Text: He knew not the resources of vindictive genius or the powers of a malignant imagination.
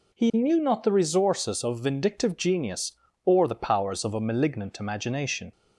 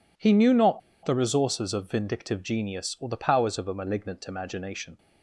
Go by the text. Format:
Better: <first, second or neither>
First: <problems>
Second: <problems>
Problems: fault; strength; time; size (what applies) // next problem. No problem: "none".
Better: first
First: none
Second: pauses between "not" and "the"; slight; at 0.8 s; 0.25 s long